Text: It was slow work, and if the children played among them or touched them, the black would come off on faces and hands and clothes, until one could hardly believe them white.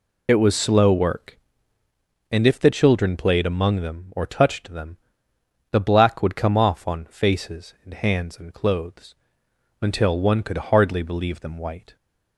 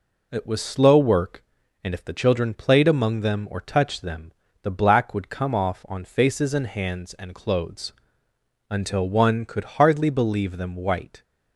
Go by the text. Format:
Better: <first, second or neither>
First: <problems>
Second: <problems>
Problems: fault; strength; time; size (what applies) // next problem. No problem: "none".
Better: second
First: loses the start of "It"; at 0.2 s; 55 ms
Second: none